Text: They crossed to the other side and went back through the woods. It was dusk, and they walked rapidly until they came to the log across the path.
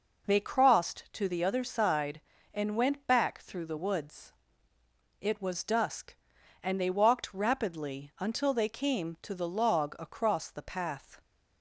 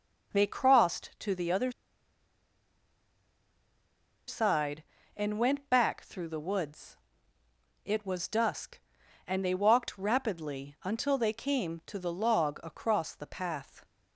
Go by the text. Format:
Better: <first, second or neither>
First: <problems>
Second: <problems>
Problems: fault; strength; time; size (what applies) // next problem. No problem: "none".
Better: first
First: none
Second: pauses between "other" and "side"; strong; at 1.7 s; 2.5 s long